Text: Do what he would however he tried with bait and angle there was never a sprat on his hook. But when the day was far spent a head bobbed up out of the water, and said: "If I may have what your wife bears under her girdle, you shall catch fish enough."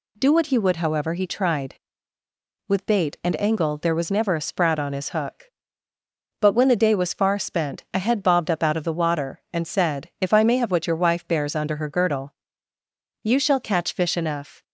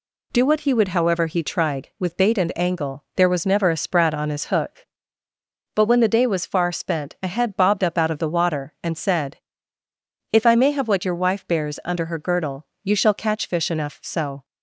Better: first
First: none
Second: goes on to say "So"; slight; from 14.0 s on; 0.42 s long

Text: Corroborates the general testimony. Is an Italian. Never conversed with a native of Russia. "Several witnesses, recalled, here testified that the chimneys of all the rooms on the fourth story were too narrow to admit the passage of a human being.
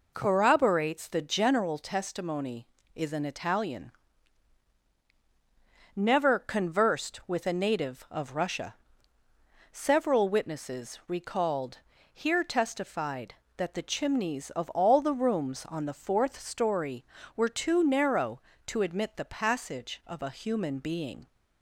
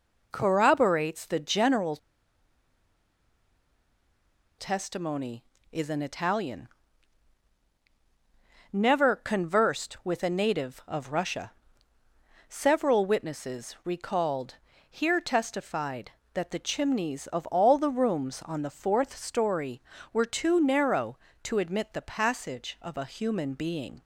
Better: first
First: none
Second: pauses between "general" and "testimony"; strong; at 1.9 s; 2.6 s long

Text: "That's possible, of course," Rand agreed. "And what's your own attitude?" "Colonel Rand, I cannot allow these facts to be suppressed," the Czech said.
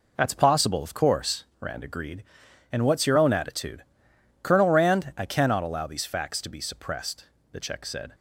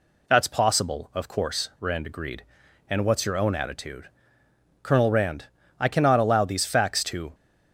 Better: first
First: none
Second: stops before "be suppressed the Czech said"; at 7.3 s

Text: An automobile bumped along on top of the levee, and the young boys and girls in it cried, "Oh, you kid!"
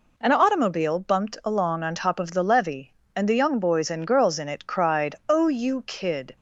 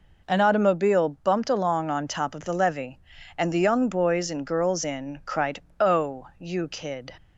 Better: first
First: none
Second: skips "it"; at 5.2 s

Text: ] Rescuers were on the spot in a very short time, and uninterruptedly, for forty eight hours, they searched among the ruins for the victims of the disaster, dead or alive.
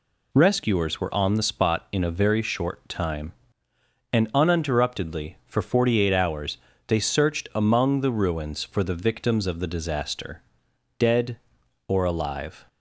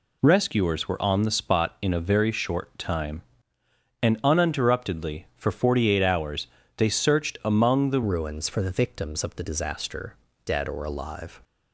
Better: first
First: none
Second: changes voice at "ruins"; from 8.0 s on; 3.4 s long

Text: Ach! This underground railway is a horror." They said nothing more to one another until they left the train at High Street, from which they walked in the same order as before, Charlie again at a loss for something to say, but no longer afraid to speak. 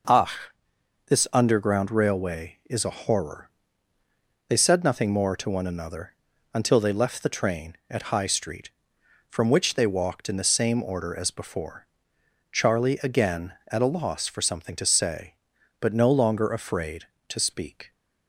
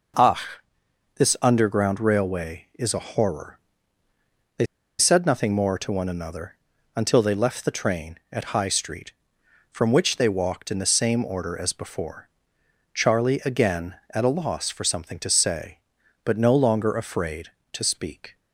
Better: first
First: pauses between "another" and "until"; at 6.1 s; 0.40 s long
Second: pauses between "They" and "said"; slight; at 4.6 s; 0.34 s long // pauses between "another" and "until"; at 6.5 s; 0.40 s long

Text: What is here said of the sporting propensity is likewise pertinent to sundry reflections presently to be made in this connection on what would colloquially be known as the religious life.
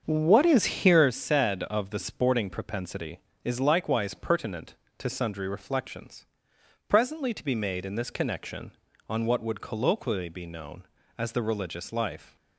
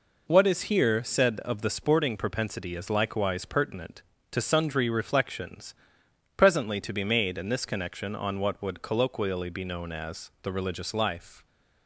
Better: second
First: starts louder than the rest; until 1.1 s; 7 dB // pauses between "reflections" and "presently"; noticeable; at 6.2 s; 0.64 s long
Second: pauses between "reflections" and "presently"; noticeable; at 5.7 s; 0.62 s long

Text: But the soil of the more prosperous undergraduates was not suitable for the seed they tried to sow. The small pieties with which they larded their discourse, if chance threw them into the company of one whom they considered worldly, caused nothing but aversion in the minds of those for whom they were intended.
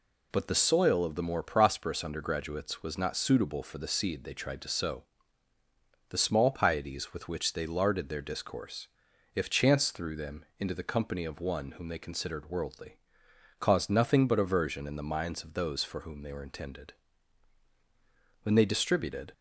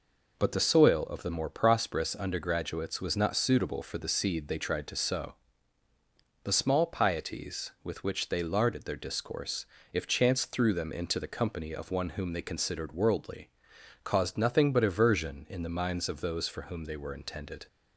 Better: second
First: goes on to say "When they distributed"; noticeable; from 18.4 s on; 0.90 s long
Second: none

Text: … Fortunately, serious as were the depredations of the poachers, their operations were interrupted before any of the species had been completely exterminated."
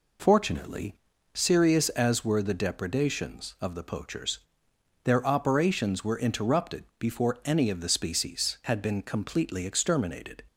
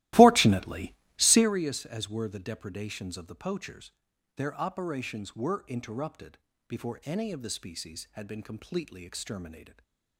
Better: first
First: none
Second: starts louder than the rest; strong; until 1.5 s; 16.5 dB // pauses between "interrupted" and "before"; slight; at 6.3 s; 0.30 s long // stays silent after the last word; slight; from 9.6 s on; 0.5 s long

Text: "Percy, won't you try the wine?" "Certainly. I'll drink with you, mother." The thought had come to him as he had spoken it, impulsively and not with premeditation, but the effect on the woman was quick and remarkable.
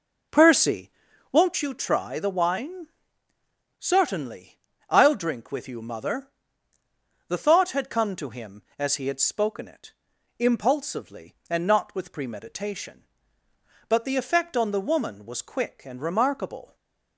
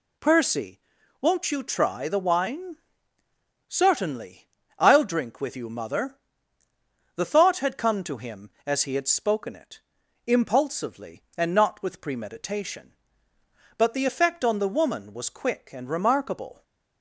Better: second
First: starts louder than the rest; noticeable; until 1.6 s; 4.5 dB // stays silent after the last word; slight; from 16.6 s on; 0.5 s long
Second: none

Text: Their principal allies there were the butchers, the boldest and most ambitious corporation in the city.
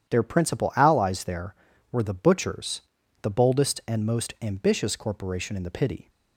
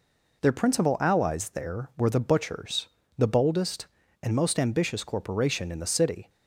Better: second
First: starts louder than the rest; strong; until 1.1 s; 9.5 dB // says "pity" for "city"; at 5.6 s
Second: none

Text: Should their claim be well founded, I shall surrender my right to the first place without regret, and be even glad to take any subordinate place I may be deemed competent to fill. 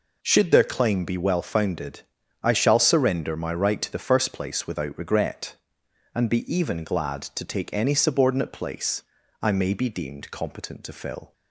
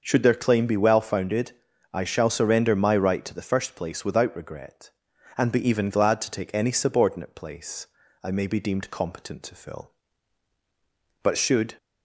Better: first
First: pauses between "place" and "I"; at 9.0 s; 0.40 s long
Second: starts louder than the rest; noticeable; until 1.0 s; 6 dB // pauses between "place" and "I"; slight; at 7.8 s; 0.36 s long // goes on to say "But should"; from 11.2 s on; 0.52 s long

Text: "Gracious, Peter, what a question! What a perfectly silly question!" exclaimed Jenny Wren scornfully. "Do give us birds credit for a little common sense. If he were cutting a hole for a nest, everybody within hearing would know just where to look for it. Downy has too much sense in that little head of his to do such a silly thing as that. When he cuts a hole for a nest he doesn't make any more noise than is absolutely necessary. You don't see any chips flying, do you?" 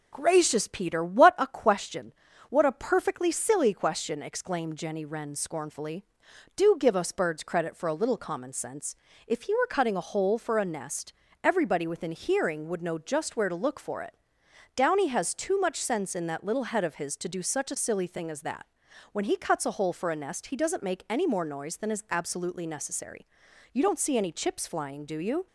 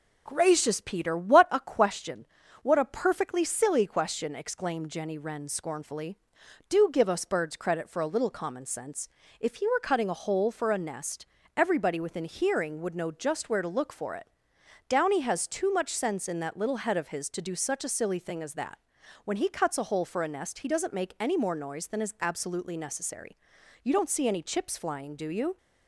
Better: neither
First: none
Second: none

